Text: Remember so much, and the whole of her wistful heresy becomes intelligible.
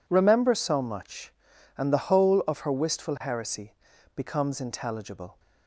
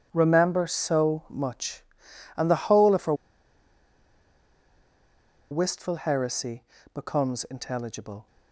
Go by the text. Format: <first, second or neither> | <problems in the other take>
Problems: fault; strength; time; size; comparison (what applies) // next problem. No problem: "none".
first | pauses between "her" and "wistful"; strong; at 3.1 s; 2.3 s long // pauses between "heresy" and "becomes"; slight; at 6.6 s; 0.30 s long; also in the first